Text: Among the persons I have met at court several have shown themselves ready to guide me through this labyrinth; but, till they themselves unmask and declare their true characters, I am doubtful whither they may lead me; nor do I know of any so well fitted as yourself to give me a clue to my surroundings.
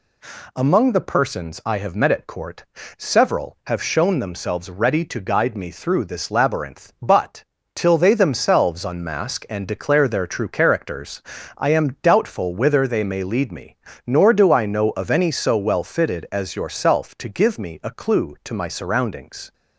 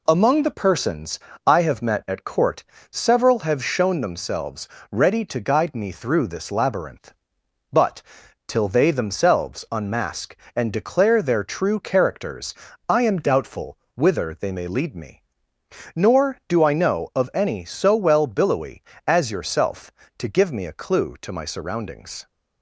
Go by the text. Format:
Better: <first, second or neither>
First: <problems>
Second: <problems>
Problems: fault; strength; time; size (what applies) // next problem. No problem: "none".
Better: first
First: pauses between "court" and "several"; slight; at 2.6 s; 0.32 s long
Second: pauses between "persons" and "I"; slight; at 1.1 s; 0.30 s long // pauses between "court" and "several"; slight; at 2.6 s; 0.30 s long // pauses between "themselves" and "ready"; slight; at 4.6 s; 0.24 s long // pauses between "doubtful" and "whither"; slight; at 13.7 s; 0.18 s long // says "billowy" for "fitted"; at 18.2 s